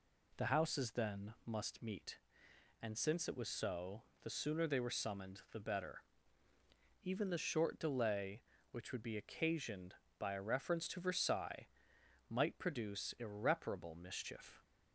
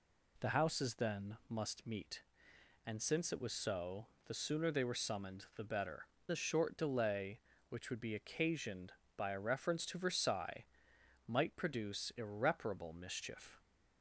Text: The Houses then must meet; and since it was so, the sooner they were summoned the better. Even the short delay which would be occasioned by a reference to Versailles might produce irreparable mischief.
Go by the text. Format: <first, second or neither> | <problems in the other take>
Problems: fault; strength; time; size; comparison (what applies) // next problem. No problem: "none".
first | skips "Even"; at 6.1 s // pauses between "Versailles" and "might"; noticeable; at 10.6 s; 0.64 s long; noticeable in the first